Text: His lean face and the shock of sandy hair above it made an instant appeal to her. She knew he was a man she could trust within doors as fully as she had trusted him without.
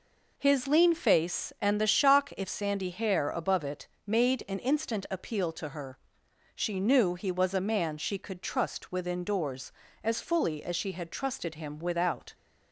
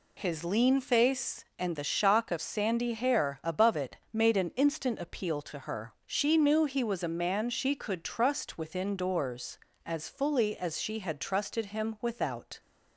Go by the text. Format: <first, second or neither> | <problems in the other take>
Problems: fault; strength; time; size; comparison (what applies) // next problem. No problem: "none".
second | says "if" for "of"; at 2.3 s // pauses between "it" and "made"; slight; at 3.8 s; 0.20 s long